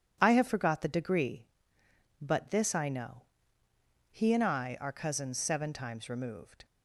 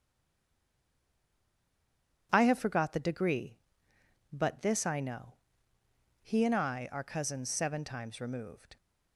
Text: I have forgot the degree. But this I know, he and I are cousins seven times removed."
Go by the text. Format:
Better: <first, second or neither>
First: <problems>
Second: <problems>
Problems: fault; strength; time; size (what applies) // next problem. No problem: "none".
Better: first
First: none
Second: stays silent before the first word; until 2.3 s; 2.3 s long